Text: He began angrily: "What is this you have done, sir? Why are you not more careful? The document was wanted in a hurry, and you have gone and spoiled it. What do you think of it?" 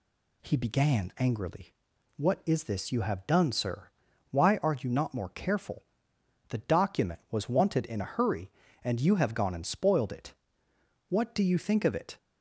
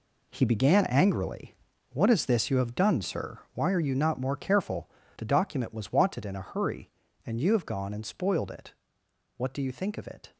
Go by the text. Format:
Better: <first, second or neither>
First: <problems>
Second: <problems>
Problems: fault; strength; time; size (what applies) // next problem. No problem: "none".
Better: first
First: none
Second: gets quieter; strong; throughout; 10.5 dB